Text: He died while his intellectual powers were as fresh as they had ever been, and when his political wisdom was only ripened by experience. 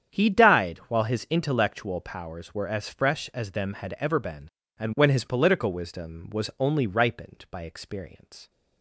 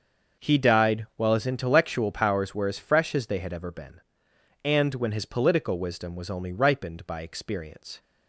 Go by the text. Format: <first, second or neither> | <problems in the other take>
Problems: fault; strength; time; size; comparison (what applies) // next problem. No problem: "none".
second | starts louder than the rest; strong; until 1.2 s; 8.5 dB; also in the second // says "them" for "they"; at 3.5 s